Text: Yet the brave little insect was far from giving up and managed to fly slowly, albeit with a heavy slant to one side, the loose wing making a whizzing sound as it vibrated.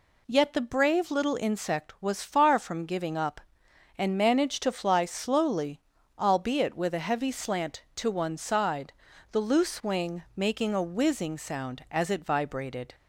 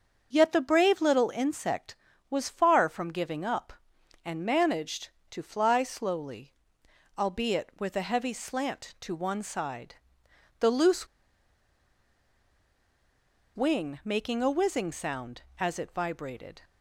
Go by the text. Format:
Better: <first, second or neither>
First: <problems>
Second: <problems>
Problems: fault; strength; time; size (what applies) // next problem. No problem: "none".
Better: first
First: none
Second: starts louder than the rest; until 1.3 s; 6 dB // pauses between "loose" and "wing"; strong; at 11.0 s; 2.4 s long